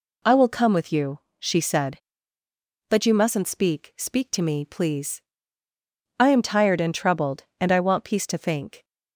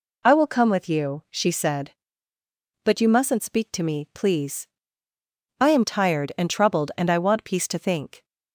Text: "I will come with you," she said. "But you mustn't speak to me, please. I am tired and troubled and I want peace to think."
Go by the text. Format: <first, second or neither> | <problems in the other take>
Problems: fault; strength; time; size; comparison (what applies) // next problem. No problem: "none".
second | says "speak" twice; at 3.9 s